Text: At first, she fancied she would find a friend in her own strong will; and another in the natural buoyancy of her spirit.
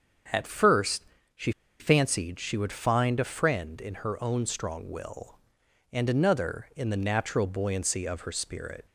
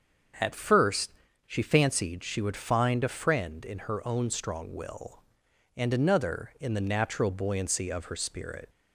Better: second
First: starts louder than the rest; strong; until 1.9 s; 7 dB // pauses between "she" and "fancied"; slight; at 1.5 s; 0.29 s long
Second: starts louder than the rest; until 1.7 s; 7 dB

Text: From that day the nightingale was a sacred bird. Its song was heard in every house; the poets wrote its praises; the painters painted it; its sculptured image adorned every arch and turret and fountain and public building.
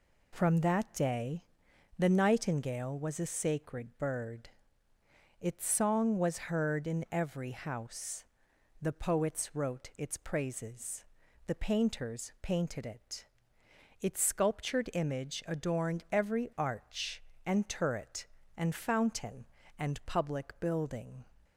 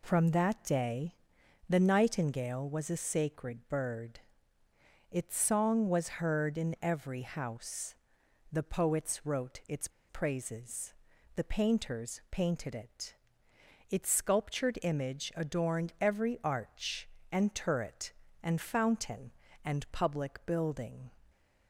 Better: first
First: pauses between "day" and "the"; noticeable; at 1.4 s; 0.52 s long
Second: pauses between "day" and "the"; noticeable; at 1.1 s; 0.52 s long // pauses between "its" and "praises"; slight; at 9.8 s; 0.20 s long

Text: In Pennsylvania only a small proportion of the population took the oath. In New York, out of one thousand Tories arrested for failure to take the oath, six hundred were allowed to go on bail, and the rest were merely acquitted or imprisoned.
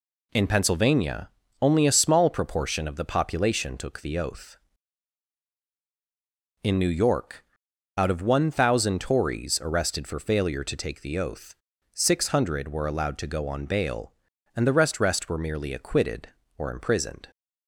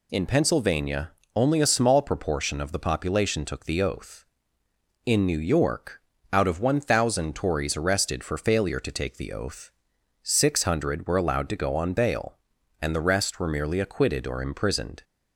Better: second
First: pauses between "Pennsylvania" and "only"; slight; at 1.2 s; 0.32 s long // says "rest" twice; at 14.9 s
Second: pauses between "Pennsylvania" and "only"; slight; at 1.1 s; 0.24 s long

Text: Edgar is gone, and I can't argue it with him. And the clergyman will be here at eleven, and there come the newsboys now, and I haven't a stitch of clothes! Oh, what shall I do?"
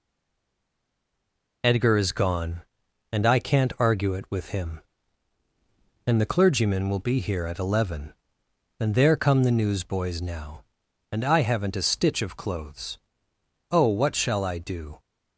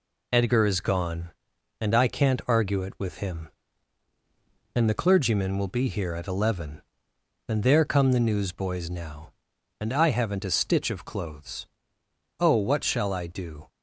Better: second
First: stays silent before the first word; noticeable; until 1.6 s; 1.6 s long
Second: none

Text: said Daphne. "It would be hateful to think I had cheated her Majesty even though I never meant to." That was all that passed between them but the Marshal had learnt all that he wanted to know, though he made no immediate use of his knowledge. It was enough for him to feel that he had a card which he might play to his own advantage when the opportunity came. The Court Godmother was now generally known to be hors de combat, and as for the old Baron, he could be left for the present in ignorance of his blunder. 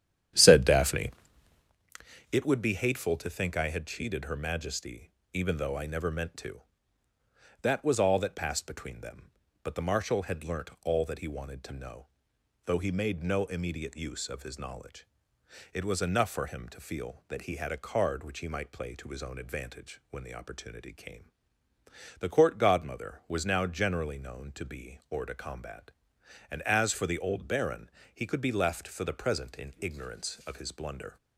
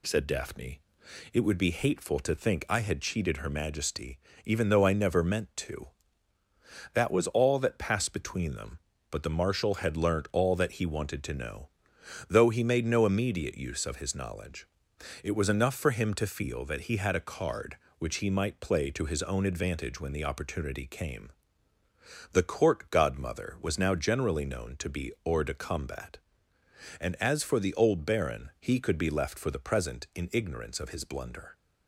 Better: second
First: starts louder than the rest; strong; until 1.8 s; 10.5 dB // pauses between "Majesty" and "even"; slight; at 5.1 s; 0.22 s long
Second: pauses between "Majesty" and "even"; slight; at 4.1 s; 0.26 s long

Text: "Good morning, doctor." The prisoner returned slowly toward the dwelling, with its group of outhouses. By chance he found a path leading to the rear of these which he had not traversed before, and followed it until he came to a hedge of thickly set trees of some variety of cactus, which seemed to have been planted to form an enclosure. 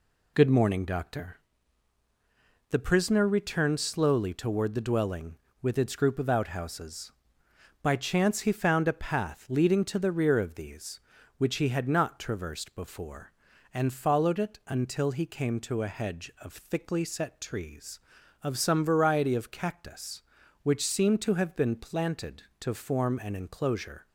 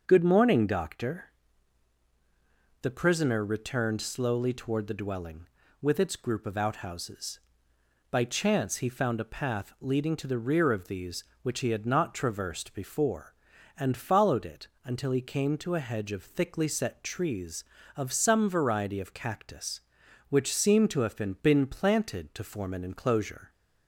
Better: first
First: none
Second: starts louder than the rest; noticeable; until 1.0 s; 6 dB // pauses between "it" and "until"; slight; at 14.6 s; 0.16 s long // says "been" twice; at 21.4 s

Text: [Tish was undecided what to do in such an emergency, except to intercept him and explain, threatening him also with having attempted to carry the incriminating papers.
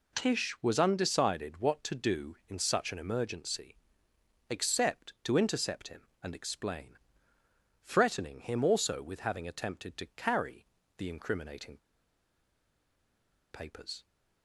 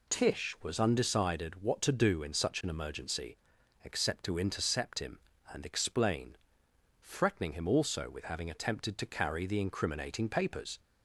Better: second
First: pauses between "carry" and "the"; slight; at 10.6 s; 0.32 s long // pauses between "incriminating" and "papers"; strong; at 11.7 s; 1.7 s long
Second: none

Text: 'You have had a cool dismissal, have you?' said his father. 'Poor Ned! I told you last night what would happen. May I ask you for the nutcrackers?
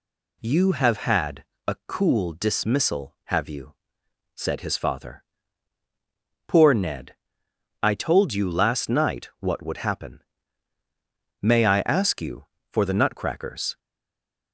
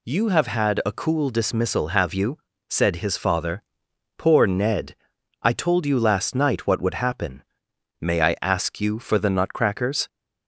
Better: second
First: pauses between "had" and "a"; slight; at 1.4 s; 0.24 s long // stays silent after the last word; slight; from 13.7 s on; 0.8 s long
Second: none

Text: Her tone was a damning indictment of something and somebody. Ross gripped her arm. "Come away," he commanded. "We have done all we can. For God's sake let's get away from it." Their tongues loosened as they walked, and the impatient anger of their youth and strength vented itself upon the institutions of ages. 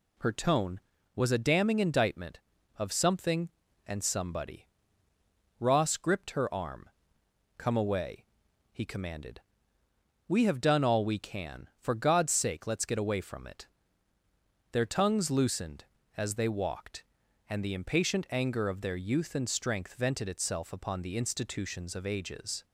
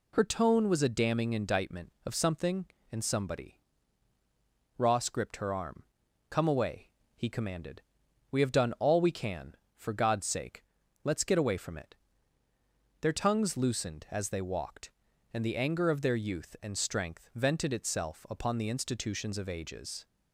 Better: first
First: none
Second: pauses between "sake" and "let's"; at 10.6 s; 0.40 s long // skips "impatient"; at 15.5 s

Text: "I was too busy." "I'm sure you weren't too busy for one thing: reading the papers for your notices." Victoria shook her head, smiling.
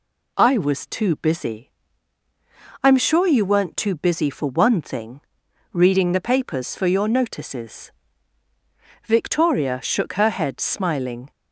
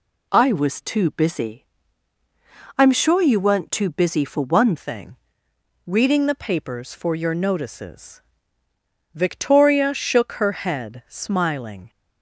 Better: first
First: none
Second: changes voice at "thing"; from 4.7 s on; 7.1 s long

